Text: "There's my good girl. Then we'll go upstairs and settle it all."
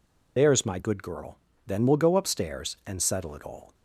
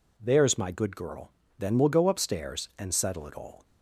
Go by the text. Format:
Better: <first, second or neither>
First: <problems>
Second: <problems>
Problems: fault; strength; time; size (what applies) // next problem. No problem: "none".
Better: second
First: loses the start of "There's"; at 0.3 s; 100 ms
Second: none